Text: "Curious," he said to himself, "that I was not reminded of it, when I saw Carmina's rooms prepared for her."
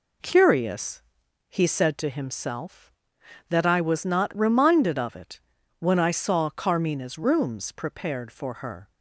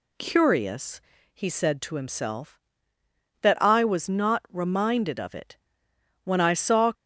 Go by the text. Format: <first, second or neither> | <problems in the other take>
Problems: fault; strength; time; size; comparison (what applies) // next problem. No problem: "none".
first | stops before "Carmina's rooms prepared for her"; at 6.9 s